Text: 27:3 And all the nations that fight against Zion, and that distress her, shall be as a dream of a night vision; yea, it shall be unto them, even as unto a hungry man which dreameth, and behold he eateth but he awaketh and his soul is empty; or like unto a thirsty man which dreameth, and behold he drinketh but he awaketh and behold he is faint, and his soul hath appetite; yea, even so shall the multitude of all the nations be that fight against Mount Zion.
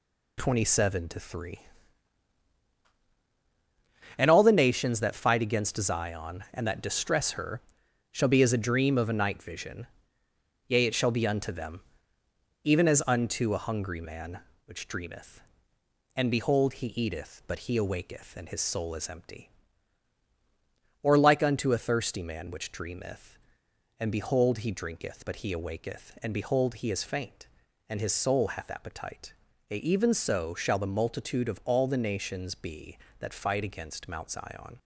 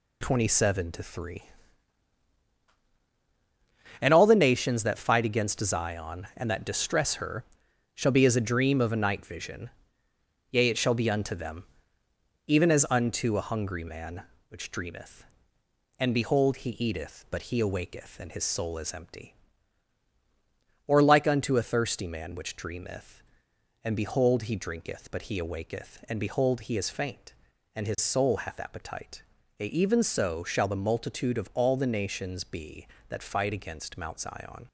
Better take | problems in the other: neither | none

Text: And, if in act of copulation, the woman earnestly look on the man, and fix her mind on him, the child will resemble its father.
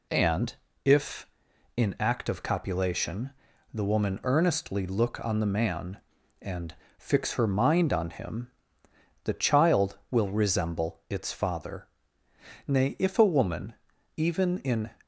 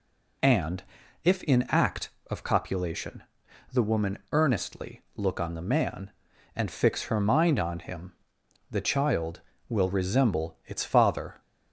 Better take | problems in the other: second | pauses between "and" and "fix"; slight; at 6.7 s; 0.24 s long // goes on to say "Nay if a woman even in"; strong; from 12.6 s on; 2.2 s long

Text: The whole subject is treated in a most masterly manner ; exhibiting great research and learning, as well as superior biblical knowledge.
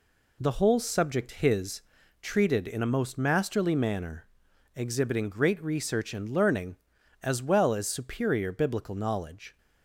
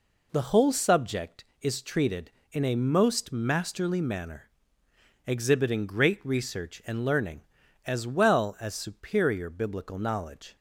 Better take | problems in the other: second | says "his" for "is"; at 1.3 s

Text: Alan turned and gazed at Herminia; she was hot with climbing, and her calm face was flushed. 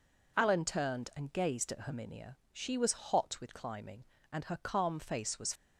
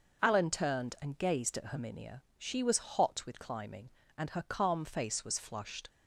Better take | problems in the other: second | stops before "flushed"; at 5.5 s

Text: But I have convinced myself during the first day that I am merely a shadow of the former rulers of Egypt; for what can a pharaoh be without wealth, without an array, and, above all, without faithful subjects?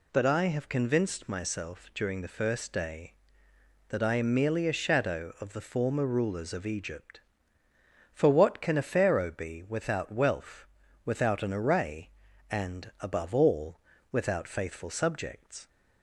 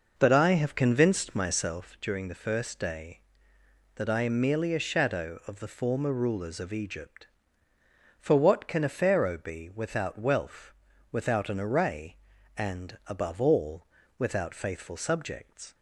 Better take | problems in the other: first | starts louder than the rest; noticeable; until 2.0 s; 5.5 dB

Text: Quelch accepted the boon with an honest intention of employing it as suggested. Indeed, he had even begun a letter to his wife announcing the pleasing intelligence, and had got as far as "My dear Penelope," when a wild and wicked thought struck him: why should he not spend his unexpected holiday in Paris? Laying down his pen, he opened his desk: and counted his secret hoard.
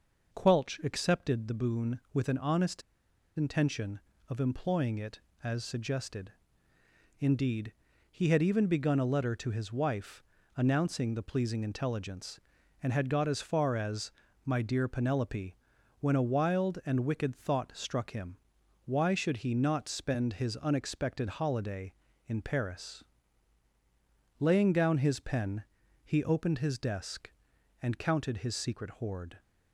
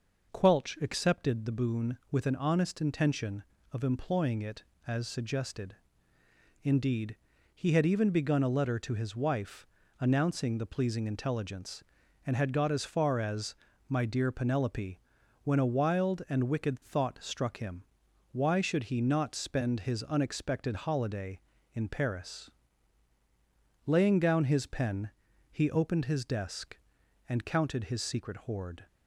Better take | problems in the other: second | pauses between "honest" and "intention"; noticeable; at 2.8 s; 0.55 s long // pauses between "wife" and "announcing"; slight; at 10.2 s; 0.34 s long; slight in the second // pauses between "as" and "My"; slight; at 14.1 s; 0.34 s long; slight in the second

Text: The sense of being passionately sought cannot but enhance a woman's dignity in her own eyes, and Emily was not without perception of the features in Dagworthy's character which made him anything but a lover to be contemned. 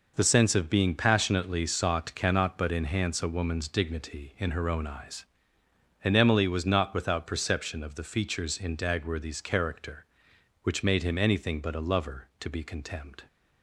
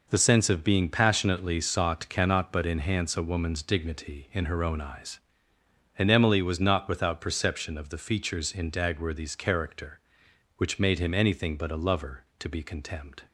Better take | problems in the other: neither | none

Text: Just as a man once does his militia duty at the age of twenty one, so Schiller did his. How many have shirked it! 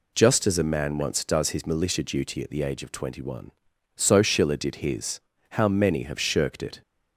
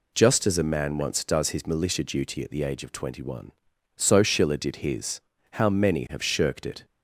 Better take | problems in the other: neither | none

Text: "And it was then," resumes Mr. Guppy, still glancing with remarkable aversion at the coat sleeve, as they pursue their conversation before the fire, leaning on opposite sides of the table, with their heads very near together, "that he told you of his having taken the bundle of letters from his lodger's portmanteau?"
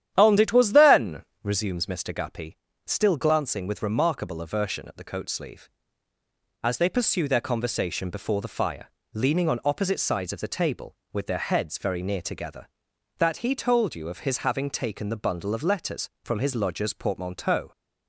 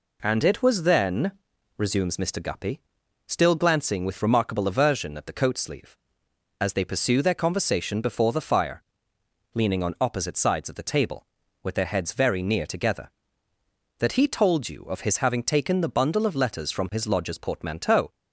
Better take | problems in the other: second | starts louder than the rest; strong; until 1.7 s; 10.5 dB

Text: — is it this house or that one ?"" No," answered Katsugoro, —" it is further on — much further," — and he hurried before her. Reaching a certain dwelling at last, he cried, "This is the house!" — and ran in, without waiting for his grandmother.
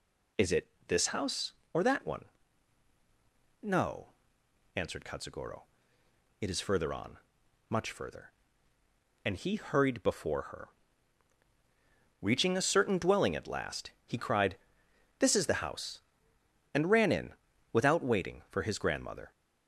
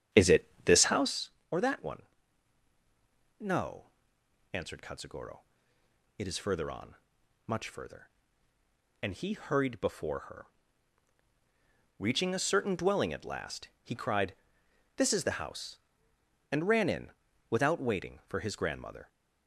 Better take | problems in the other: first | starts louder than the rest; strong; until 1.2 s; 10 dB // pauses between "it" and "this"; slight; at 0.4 s; 0.20 s long; slight in the first

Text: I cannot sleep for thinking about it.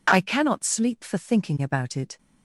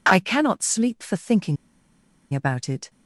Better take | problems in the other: first | pauses between "thinking" and "about"; noticeable; at 1.5 s; 0.77 s long

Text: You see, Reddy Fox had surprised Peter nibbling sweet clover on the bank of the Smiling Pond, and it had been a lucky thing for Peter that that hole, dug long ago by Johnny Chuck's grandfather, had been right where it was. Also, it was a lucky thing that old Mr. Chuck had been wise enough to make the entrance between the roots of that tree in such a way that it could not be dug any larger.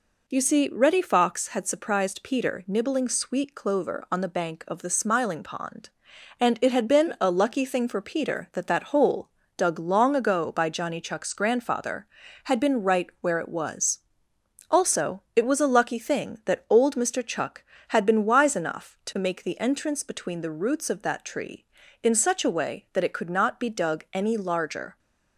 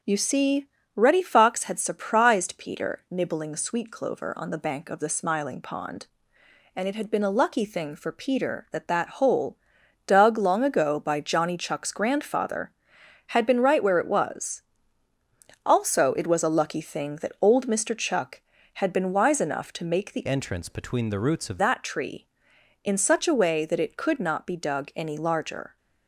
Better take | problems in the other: first | changes voice from "entrance" to "of"; from 20.2 to 21.5 s; 1.3 s long

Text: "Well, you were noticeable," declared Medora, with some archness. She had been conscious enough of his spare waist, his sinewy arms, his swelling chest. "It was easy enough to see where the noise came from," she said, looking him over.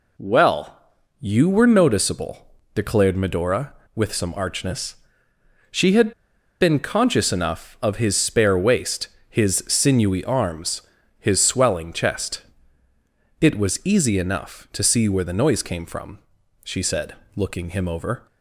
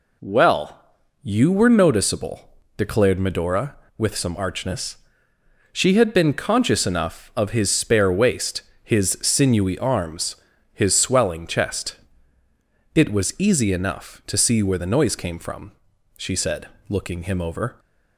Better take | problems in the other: second | pauses between "had" and "been"; noticeable; at 6.1 s; 0.48 s long

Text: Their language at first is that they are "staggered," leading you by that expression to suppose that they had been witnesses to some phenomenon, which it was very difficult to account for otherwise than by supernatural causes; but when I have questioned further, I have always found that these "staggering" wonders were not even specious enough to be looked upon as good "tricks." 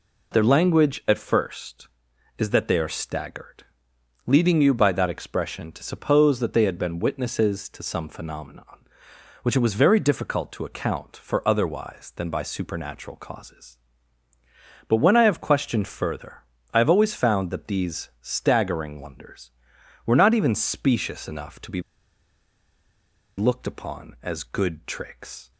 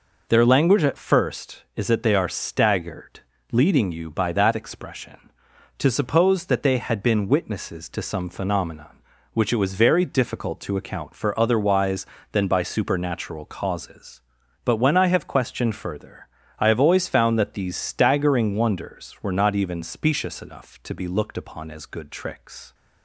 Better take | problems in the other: second | pauses between "be" and "looked"; strong; at 21.8 s; 1.5 s long

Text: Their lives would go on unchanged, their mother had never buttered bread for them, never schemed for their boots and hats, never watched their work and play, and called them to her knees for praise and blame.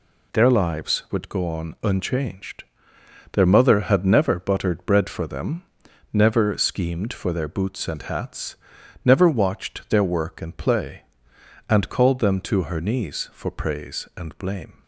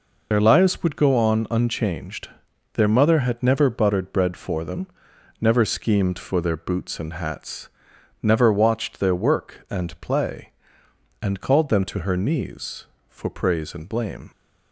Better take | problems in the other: first | loses the start of "Their"; at 0.3 s; 65 ms

